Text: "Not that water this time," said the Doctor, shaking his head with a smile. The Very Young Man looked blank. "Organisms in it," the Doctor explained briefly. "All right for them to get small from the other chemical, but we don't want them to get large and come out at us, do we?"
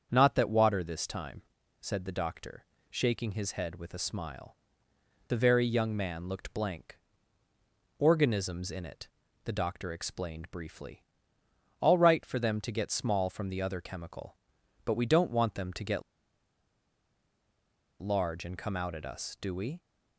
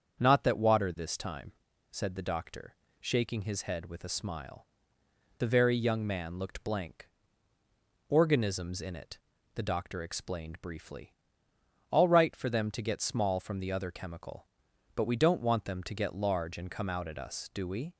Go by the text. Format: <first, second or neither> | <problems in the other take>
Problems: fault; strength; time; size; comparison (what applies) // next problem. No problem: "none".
second | starts louder than the rest; strong; until 1.1 s; 7.5 dB; strong in the second // pauses between "get" and "large"; strong; at 16.0 s; 2.0 s long